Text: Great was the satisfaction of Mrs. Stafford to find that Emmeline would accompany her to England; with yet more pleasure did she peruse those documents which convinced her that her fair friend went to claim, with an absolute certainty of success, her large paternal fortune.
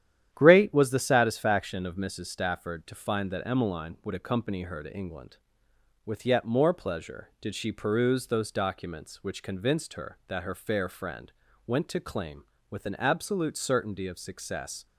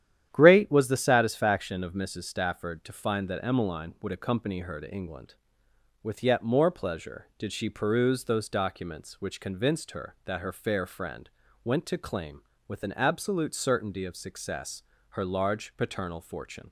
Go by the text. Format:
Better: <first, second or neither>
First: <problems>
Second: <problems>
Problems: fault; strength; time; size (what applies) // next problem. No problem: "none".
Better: second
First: starts louder than the rest; strong; until 1.3 s; 10.5 dB // pauses between "friend" and "went"; slight; at 11.3 s; 0.32 s long // stops before "her large paternal fortune"; at 14.8 s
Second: starts louder than the rest; strong; until 1.3 s; 10.5 dB // pauses between "friend" and "went"; slight; at 11.3 s; 0.32 s long